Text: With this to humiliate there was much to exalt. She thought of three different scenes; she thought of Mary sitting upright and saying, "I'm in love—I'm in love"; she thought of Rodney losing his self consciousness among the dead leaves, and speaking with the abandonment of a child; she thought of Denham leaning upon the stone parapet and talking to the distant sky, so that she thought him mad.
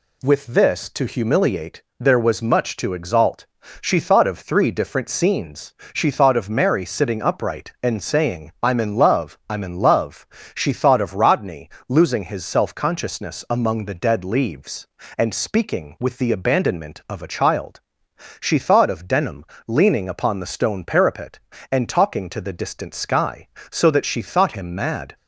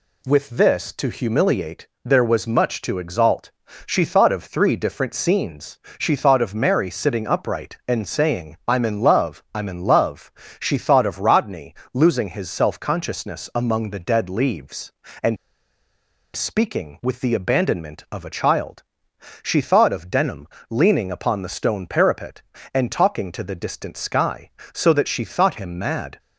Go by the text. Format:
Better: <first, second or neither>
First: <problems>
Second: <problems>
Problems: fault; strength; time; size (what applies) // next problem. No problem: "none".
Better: first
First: pauses between "humiliate" and "there"; slight; at 1.8 s; 0.16 s long // pauses between "Rodney" and "losing"; slight; at 11.6 s; 0.18 s long // pauses between "Denham" and "leaning"; slight; at 19.4 s; 0.24 s long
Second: pauses between "humiliate" and "there"; slight; at 1.8 s; 0.16 s long // pauses between "Rodney" and "losing"; slight; at 11.7 s; 0.18 s long // pauses between "and" and "speaking"; noticeable; at 15.3 s; 0.98 s long // pauses between "Denham" and "leaning"; slight; at 20.4 s; 0.24 s long